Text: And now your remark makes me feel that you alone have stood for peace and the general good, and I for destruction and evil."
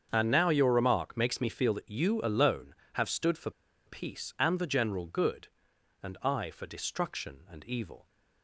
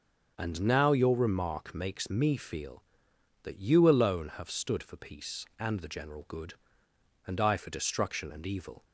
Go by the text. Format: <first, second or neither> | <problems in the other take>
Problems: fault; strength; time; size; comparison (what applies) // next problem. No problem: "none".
second | starts louder than the rest; strong; until 1.1 s; 7.5 dB; also in the second // pauses between "for" and "peace"; at 3.4 s; 0.36 s long